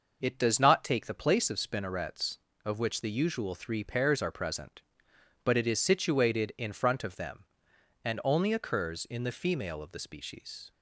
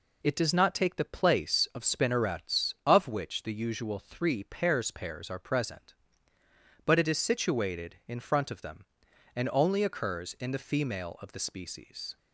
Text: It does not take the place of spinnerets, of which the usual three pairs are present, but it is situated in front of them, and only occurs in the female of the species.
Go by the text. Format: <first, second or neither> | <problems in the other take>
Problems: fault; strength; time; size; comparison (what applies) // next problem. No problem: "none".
first | says "pairs" twice; at 4.9 s